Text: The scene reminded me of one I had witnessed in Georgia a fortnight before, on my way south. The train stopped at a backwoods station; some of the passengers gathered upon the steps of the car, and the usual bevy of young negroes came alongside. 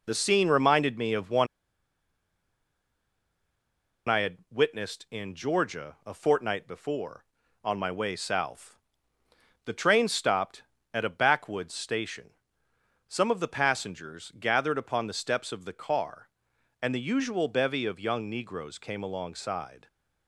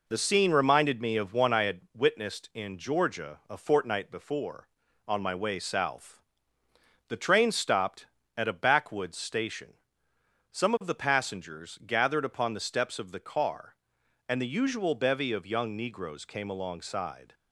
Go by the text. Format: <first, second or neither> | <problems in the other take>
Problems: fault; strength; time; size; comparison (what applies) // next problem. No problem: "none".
second | pauses between "one" and "I"; strong; at 1.4 s; 2.6 s long